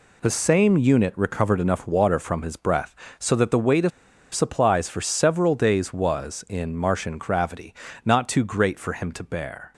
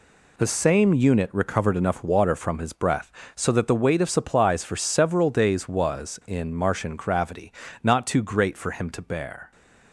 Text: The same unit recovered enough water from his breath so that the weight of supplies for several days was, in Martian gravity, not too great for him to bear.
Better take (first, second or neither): second